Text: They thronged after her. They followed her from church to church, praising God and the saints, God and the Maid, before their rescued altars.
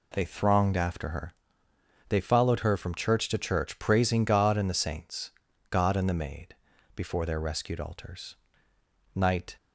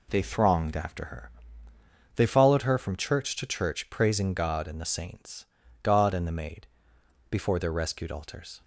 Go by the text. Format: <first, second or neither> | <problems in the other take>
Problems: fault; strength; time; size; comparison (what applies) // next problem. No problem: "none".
second | goes on to say "Night"; slight; from 9.1 s on; 0.42 s long